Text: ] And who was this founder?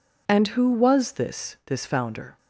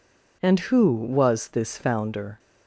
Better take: second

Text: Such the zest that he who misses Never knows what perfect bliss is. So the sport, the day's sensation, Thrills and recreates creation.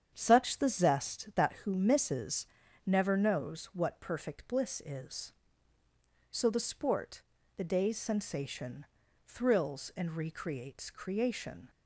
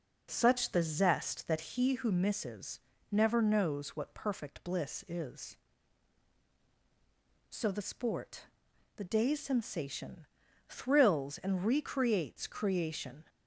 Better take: second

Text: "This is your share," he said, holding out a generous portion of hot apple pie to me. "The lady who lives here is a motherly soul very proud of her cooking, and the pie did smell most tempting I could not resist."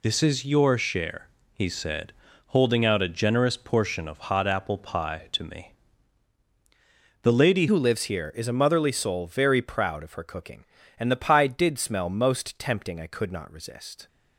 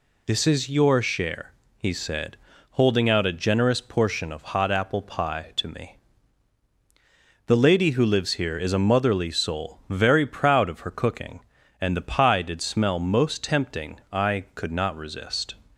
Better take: second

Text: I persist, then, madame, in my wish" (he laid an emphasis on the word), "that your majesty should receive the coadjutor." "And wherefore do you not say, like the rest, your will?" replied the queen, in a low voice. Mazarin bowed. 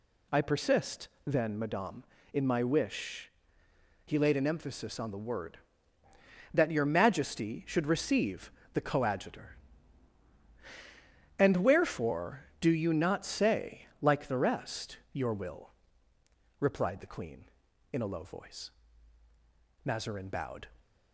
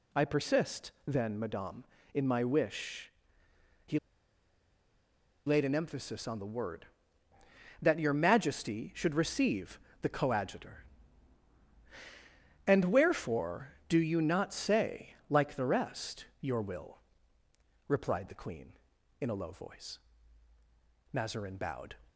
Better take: first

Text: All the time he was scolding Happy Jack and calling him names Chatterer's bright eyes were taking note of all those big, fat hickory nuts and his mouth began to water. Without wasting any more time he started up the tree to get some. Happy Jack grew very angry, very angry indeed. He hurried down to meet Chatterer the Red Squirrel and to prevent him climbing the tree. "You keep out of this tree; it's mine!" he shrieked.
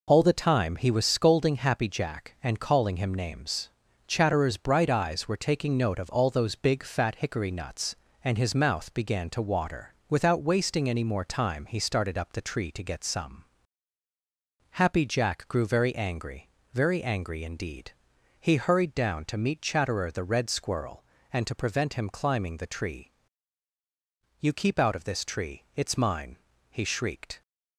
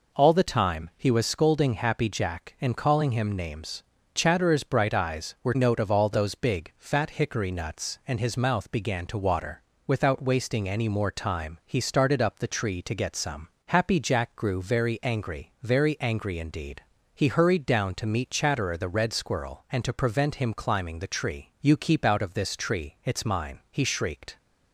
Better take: first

